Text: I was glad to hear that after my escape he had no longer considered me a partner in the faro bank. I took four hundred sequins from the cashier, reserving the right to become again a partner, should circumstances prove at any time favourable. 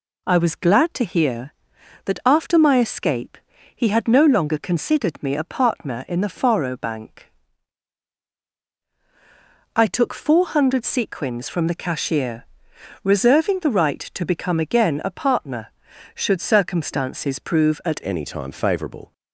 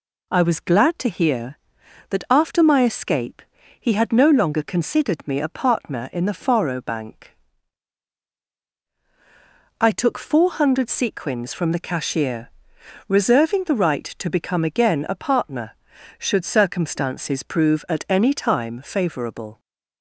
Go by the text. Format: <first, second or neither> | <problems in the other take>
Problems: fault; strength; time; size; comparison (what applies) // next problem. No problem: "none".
second | pauses between "escape" and "he"; slight; at 3.3 s; 0.36 s long; slight in the second // changes voice at "any"; from 18.0 s on; 1.1 s long